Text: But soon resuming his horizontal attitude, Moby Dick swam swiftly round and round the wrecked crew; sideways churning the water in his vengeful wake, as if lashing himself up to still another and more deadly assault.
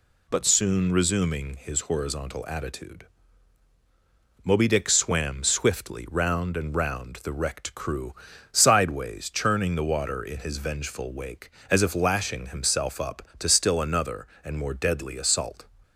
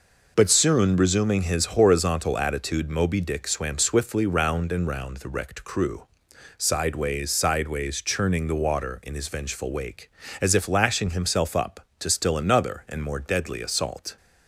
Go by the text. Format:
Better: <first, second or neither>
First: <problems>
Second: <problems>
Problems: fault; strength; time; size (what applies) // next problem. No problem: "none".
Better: first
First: none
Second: says "sideways" twice; at 7.3 s